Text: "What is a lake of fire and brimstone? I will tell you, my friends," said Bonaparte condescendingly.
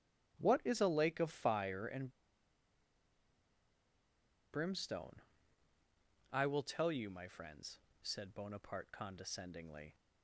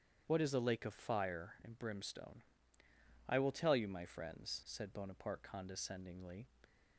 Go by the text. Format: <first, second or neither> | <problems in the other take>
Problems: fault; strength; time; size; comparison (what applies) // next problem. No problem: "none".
second | starts louder than the rest; strong; until 1.4 s; 12.5 dB; strong in the second // pauses between "and" and "brimstone"; strong; at 2.1 s; 2.4 s long